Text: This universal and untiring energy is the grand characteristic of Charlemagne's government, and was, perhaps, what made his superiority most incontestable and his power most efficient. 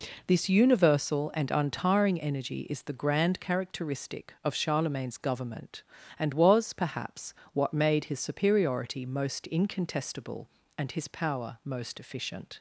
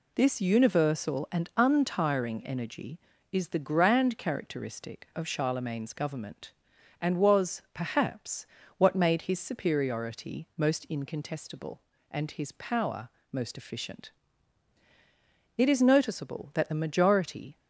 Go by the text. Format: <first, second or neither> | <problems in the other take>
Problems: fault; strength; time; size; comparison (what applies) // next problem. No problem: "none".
first | pauses between "power" and "most"; slight; at 13.0 s; 0.23 s long // goes on to say "It is noticeable that the majority"; strong; from 15.5 s on; 2.0 s long